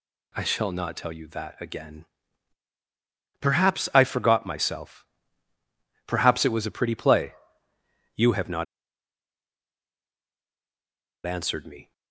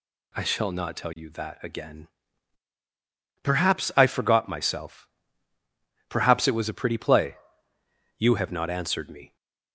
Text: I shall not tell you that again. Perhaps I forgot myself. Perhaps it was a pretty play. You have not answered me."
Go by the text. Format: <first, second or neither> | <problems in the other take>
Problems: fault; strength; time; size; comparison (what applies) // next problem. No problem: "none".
second | pauses between "not" and "answered"; strong; at 8.6 s; 2.6 s long